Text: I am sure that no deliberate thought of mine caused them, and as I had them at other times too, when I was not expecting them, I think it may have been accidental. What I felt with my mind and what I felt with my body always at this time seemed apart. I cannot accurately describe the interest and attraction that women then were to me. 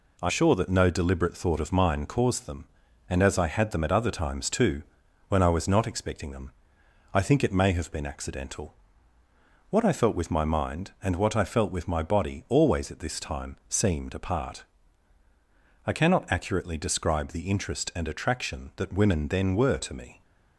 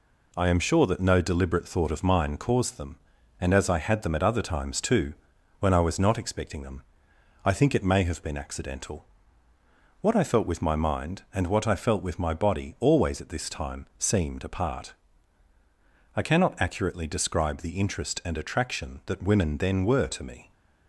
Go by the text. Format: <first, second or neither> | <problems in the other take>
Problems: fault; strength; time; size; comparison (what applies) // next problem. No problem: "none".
second | skips "am"; at 0.3 s